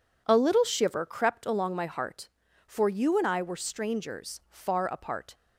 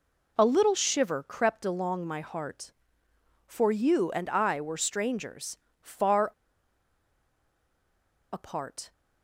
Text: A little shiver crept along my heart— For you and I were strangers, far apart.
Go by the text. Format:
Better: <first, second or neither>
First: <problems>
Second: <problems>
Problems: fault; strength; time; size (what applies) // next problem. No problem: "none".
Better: first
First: none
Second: pauses between "far" and "apart"; strong; at 6.3 s; 2.0 s long